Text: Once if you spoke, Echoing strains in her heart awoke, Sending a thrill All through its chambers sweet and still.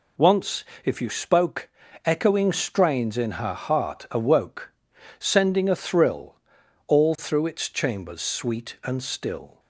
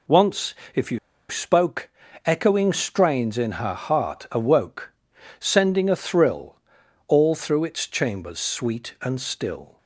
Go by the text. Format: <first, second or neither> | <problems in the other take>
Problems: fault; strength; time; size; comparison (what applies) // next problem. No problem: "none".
first | pauses between "Once" and "if"; slight; at 0.5 s; 0.20 s long; slight in the first // pauses between "you" and "spoke"; slight; at 0.9 s; 0.30 s long // pauses between "thrill" and "All"; noticeable; at 6.5 s; 0.52 s long; noticeable in the first